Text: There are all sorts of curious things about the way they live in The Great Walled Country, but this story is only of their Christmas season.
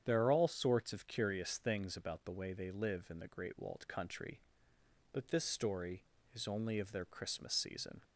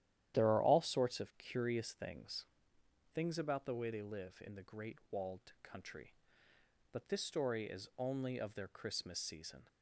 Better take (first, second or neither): first